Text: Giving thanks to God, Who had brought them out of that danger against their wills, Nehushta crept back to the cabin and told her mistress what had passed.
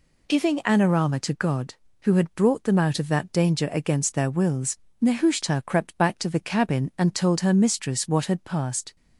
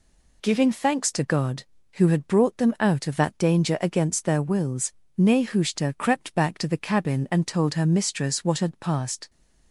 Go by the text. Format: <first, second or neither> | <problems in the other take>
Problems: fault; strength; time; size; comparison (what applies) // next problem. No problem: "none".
second | says "anorama" for "thanks"; at 0.6 s